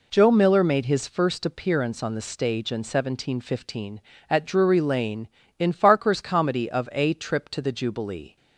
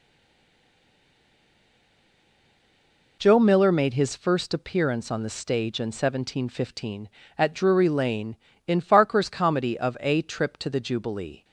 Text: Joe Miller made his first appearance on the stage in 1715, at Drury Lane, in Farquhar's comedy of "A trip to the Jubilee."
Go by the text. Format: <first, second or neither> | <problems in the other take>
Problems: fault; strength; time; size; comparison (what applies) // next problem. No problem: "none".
first | stays silent before the first word; strong; until 3.2 s; 3.2 s long